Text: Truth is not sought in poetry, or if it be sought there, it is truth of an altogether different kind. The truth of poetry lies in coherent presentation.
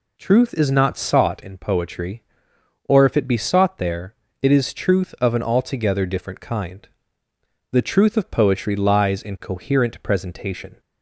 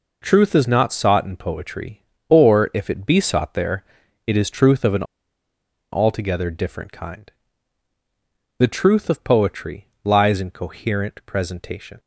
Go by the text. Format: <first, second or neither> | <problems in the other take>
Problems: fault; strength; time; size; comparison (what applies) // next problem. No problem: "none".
first | pauses between "an" and "altogether"; noticeable; at 5.0 s; 0.89 s long // pauses between "poetry" and "lies"; slight; at 9.8 s; 0.16 s long